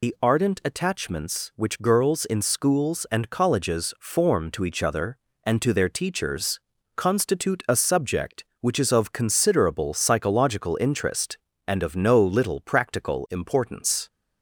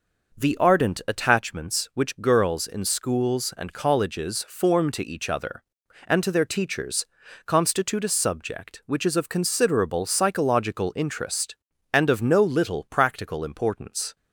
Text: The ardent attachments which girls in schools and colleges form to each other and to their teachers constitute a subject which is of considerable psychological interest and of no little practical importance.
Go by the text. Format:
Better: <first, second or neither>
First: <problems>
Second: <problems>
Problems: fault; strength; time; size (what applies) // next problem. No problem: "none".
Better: second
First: loses the start of "The"; at 0.0 s; 120 ms // pauses between "teachers" and "constitute"; slight; at 6.5 s; 0.36 s long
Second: pauses between "teachers" and "constitute"; at 7.0 s; 0.40 s long